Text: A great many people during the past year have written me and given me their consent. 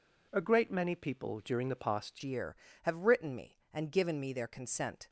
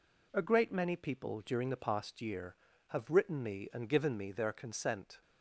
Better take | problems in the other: second | changes voice at "year"; from 2.2 s on; 2.8 s long

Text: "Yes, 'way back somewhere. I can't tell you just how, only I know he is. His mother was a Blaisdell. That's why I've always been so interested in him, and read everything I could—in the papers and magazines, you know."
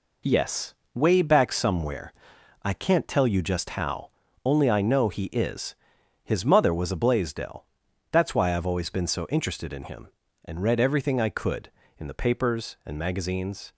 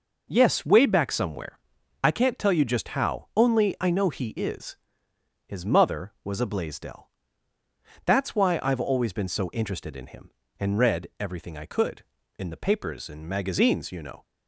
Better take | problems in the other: second | stops before "you know"; at 13.7 s

